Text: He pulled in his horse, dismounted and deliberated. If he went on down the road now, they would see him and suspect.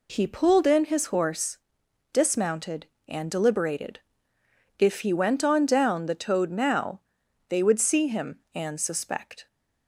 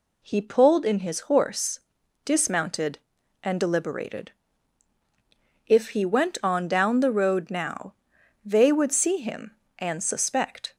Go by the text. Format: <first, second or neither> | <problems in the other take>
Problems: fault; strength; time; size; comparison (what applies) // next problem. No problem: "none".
second | says "toad" for "road"; at 6.1 s